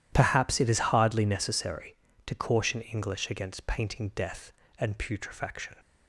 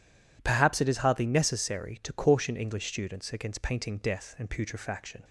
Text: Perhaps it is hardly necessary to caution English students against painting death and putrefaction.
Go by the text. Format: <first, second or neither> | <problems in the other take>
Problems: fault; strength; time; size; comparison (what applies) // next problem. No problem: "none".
second | skips "students"; at 3.3 s